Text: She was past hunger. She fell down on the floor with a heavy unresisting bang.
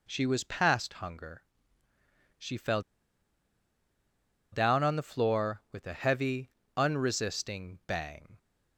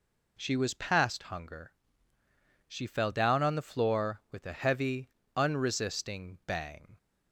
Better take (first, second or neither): second